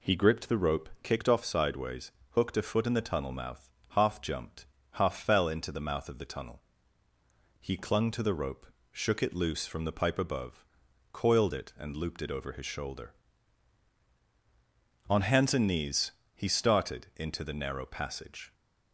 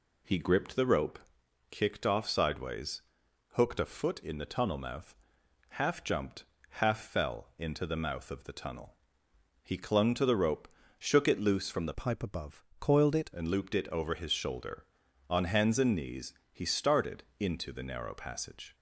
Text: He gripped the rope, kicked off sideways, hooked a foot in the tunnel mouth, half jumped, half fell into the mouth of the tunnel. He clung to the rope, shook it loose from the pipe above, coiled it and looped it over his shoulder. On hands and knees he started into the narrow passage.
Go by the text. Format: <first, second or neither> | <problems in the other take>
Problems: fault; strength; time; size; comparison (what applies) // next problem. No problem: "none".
first | changes voice from "pipe" to "it"; from 11.9 to 13.3 s; 1.4 s long // pauses between "knees" and "he"; slight; at 16.3 s; 0.18 s long; slight in the first // pauses between "started" and "into"; slight; at 17.2 s; 0.16 s long